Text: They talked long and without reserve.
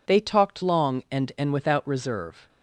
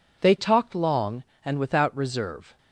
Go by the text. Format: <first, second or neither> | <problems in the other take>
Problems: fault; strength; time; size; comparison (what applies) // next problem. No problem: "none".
second | says "and" twice; at 1.3 s